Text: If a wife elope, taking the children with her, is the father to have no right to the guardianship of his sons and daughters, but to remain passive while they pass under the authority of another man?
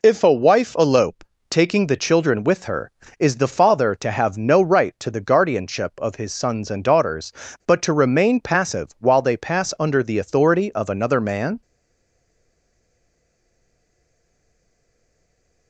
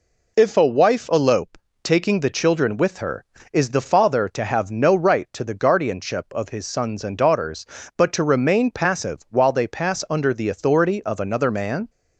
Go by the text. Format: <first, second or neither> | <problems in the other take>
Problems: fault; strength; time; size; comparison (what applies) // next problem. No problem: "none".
second | stays silent after the last word; strong; from 11.6 s on; 4.0 s long